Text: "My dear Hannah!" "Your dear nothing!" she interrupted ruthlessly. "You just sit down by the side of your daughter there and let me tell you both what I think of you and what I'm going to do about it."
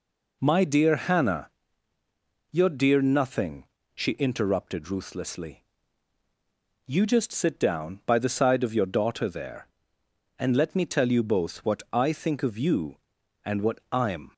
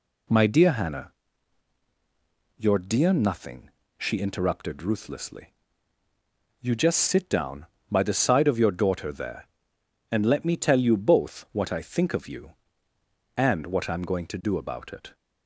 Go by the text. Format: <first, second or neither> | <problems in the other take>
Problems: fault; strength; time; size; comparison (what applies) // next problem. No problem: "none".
second | stops before "going to do about it"; at 14.3 s